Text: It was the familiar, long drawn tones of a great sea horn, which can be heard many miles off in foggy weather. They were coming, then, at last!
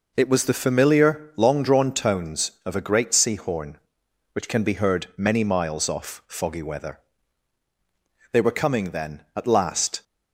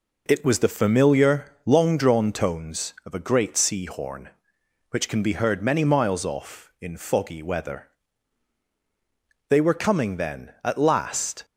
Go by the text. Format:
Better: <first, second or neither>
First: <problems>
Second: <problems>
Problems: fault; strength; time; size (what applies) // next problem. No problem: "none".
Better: second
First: skips "in"; at 6.2 s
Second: none